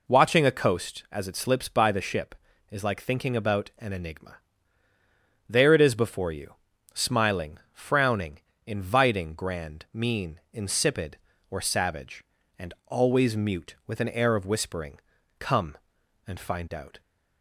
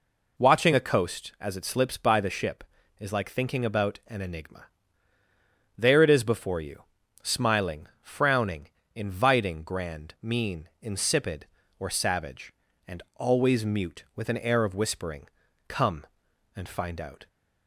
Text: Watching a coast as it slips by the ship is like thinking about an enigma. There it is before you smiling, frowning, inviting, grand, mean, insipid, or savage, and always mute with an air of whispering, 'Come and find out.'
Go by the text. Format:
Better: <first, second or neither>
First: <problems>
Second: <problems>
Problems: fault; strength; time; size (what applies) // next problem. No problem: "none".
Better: neither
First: pauses between "you" and "smiling"; at 6.5 s; 0.40 s long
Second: pauses between "you" and "smiling"; at 6.8 s; 0.40 s long